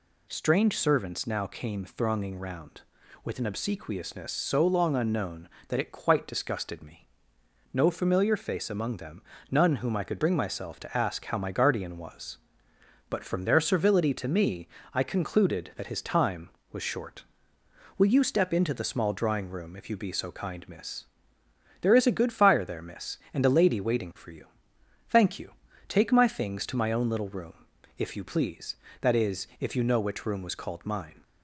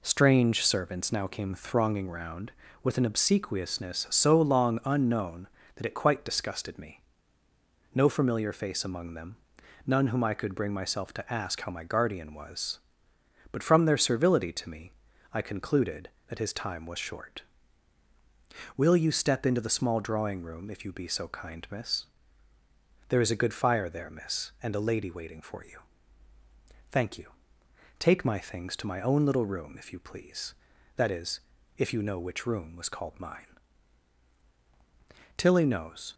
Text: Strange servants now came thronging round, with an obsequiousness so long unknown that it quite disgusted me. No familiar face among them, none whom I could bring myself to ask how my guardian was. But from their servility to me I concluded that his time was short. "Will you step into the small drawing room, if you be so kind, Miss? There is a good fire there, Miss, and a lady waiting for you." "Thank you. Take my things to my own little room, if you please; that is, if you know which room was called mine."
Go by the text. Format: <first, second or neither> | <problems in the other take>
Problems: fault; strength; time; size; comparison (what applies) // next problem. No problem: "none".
first | pauses between "me" and "I"; at 14.9 s; 0.42 s long; slight in the first // goes on to say "Tilly knows"; noticeable; from 35.3 s on; 0.78 s long